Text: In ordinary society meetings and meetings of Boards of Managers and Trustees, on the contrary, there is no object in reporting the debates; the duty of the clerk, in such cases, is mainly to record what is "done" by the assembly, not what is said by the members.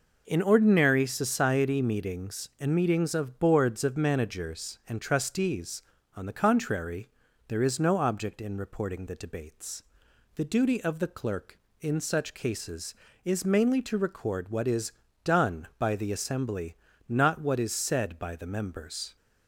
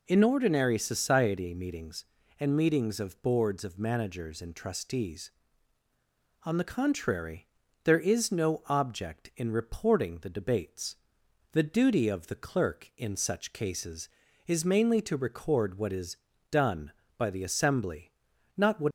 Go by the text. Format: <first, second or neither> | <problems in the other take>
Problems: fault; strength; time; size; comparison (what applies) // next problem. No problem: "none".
first | pauses between "is" and "done"; slight; at 16.1 s; 0.34 s long; slight in the first // stops before "is said by the members"; at 18.8 s